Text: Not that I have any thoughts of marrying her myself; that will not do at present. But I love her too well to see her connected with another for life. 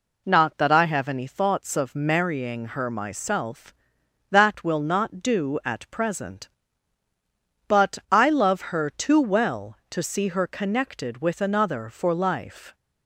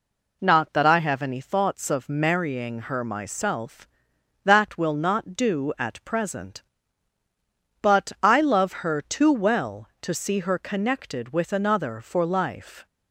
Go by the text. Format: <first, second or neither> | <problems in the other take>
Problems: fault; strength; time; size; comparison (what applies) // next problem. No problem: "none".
neither | none